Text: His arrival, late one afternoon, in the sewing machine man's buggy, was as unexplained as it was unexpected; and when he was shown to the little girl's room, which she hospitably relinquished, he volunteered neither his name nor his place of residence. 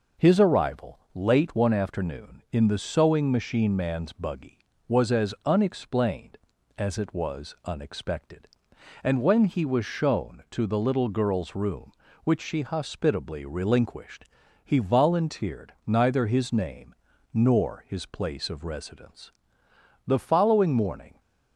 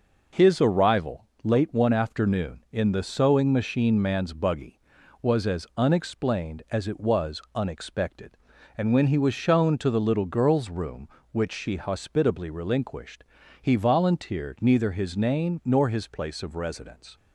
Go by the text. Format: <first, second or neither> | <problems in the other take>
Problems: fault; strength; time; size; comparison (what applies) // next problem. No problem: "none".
second | pauses between "name" and "nor"; slight; at 16.9 s; 0.36 s long // goes on to say "The following morning"; noticeable; from 20.0 s on; 1.1 s long